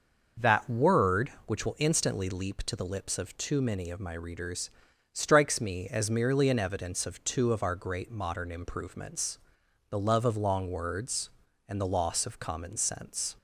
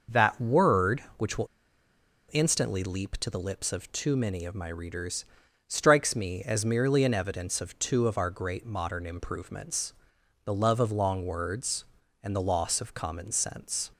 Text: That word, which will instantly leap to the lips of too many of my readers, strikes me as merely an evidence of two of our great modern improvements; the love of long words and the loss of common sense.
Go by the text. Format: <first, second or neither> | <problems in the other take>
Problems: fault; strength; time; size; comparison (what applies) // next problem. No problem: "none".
first | starts louder than the rest; noticeable; until 1.2 s; 6 dB; noticeable in the first // pauses between "will" and "instantly"; noticeable; at 1.4 s; 0.85 s long